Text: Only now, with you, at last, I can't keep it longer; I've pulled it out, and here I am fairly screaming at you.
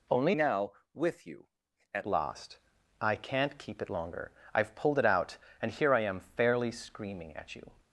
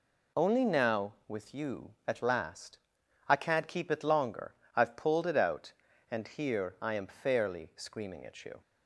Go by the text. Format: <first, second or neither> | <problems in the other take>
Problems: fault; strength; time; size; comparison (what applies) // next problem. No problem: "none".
second | changes voice from "now" to "at"; from 0.3 to 2.0 s; 1.7 s long